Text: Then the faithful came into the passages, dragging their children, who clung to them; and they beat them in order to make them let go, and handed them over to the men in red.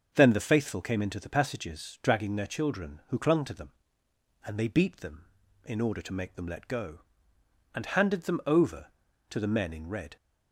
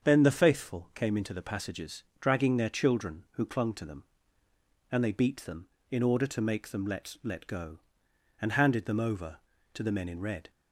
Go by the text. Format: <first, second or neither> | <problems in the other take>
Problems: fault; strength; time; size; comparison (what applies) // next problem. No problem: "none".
first | starts louder than the rest; until 1.1 s; 7 dB; also in the first // says "let" twice; at 7.2 s